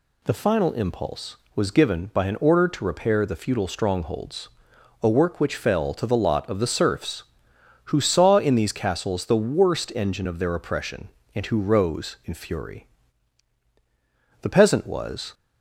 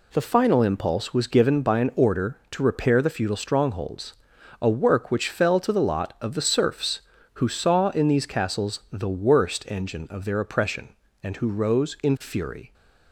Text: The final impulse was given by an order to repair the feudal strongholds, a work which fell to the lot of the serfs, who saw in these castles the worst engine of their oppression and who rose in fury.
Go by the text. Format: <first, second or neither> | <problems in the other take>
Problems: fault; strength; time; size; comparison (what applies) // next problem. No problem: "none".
second | goes on to say "The peasant was"; noticeable; from 14.4 s on; 0.92 s long